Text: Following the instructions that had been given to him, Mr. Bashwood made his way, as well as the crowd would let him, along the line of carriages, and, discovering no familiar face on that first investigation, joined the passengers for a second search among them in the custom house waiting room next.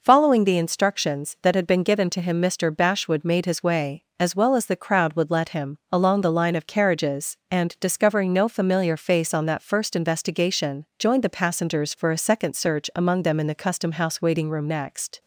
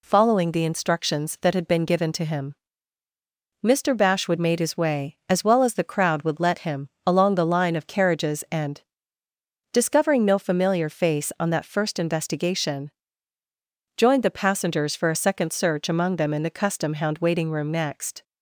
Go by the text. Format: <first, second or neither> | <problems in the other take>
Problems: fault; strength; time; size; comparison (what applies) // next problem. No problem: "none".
first | says "hound" for "house"; at 16.9 s